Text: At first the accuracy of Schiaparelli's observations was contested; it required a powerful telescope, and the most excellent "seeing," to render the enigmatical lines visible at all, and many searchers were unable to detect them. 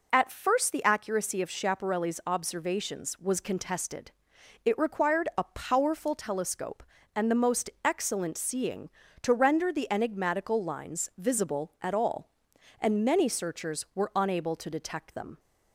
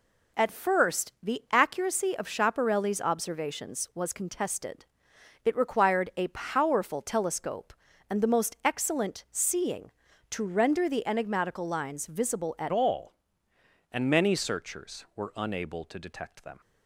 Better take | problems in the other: first | changes voice at "all"; from 12.7 s on; 3.9 s long

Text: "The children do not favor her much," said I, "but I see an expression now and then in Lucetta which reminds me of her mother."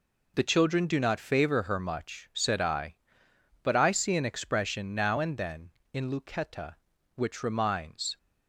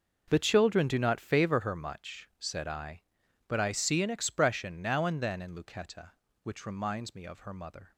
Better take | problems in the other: second | stops before "me of her mother"; at 8.1 s

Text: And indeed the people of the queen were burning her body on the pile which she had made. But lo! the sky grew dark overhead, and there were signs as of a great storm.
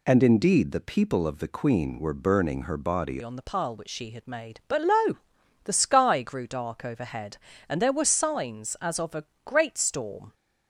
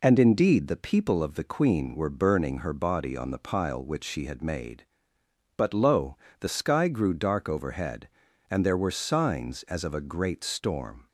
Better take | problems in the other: second | changes voice at "on"; from 3.2 s on; 7.1 s long // pauses between "a" and "great"; slight; at 9.2 s; 0.20 s long

